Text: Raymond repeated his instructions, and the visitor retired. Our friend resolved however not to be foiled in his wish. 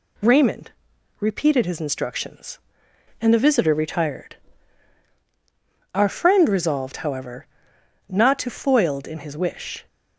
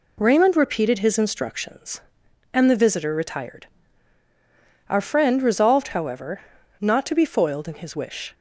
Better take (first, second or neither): second